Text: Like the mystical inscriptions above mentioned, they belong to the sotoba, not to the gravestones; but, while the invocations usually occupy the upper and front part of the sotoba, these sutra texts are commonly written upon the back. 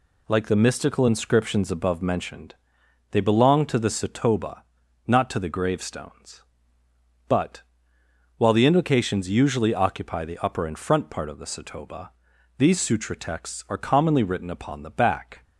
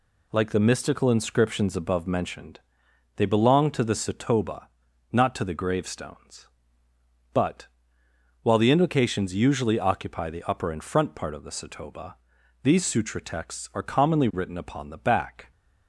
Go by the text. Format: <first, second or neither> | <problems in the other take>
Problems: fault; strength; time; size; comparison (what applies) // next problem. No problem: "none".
neither | none